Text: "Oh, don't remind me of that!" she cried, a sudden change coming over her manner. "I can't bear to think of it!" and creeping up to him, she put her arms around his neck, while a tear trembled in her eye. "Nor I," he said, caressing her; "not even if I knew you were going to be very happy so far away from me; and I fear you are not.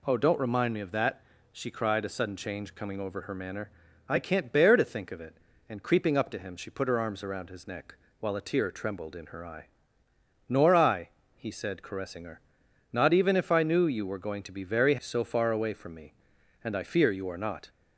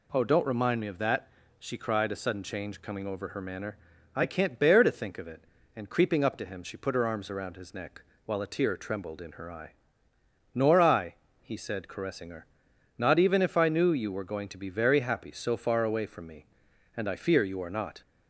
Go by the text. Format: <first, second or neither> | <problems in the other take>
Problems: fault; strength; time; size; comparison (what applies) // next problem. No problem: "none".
second | skips "happy"; at 14.9 s